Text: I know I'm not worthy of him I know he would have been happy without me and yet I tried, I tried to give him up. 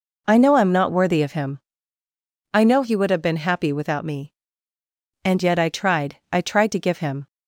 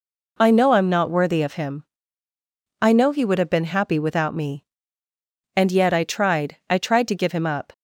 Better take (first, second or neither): second